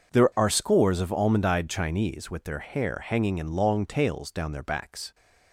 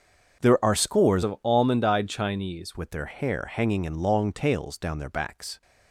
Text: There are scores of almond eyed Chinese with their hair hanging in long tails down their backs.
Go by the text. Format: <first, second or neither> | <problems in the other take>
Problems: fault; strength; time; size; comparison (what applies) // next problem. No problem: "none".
first | starts louder than the rest; until 1.4 s; 6.5 dB // changes voice from "of" to "Chinese"; from 1.2 to 2.7 s; 1.5 s long